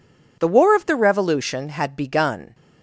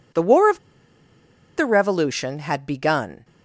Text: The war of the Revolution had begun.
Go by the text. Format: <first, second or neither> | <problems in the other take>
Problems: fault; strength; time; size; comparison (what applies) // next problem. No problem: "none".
first | pauses between "of" and "the"; at 0.5 s; 0.98 s long